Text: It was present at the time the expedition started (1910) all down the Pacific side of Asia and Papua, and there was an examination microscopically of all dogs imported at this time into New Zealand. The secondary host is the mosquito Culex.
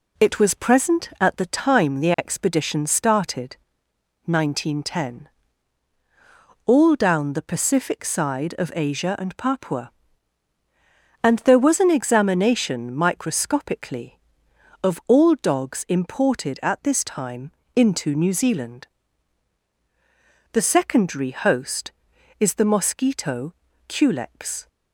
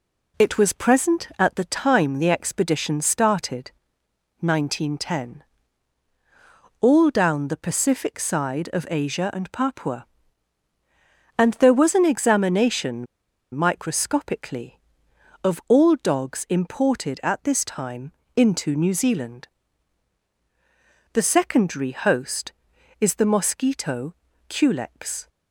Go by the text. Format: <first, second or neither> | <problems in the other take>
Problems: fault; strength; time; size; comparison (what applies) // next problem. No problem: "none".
first | pauses between "examination" and "microscopically"; noticeable; at 13.0 s; 0.48 s long // pauses between "time" and "into"; slight; at 18.1 s; 0.22 s long; slight in the first // pauses between "mosquito" and "Culex"; slight; at 24.1 s; 0.34 s long; slight in the first